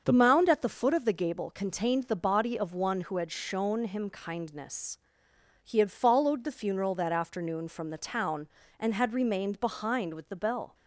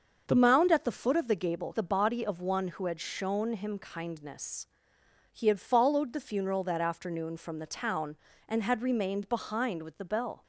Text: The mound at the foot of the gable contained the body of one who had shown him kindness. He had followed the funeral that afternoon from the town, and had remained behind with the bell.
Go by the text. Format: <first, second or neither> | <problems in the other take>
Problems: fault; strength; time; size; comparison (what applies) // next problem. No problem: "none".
first | starts louder than the rest; until 1.2 s; 6.5 dB; also in the first // skips "contained"; at 1.7 s